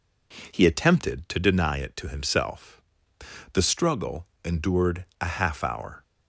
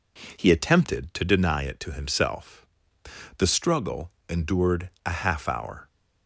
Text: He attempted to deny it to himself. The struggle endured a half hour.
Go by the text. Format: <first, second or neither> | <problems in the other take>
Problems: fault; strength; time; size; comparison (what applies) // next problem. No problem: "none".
neither | pauses between "struggle" and "endured"; slight; the same in both // pauses between "endured" and "a"; slight; the same in both